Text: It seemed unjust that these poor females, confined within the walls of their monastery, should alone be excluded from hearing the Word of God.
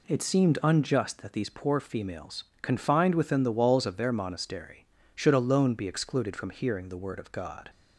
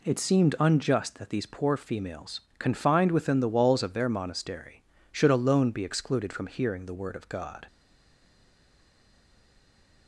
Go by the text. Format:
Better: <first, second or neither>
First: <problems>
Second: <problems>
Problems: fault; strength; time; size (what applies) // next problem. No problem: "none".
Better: first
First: none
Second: stays silent after the last word; from 7.6 s on; 2.4 s long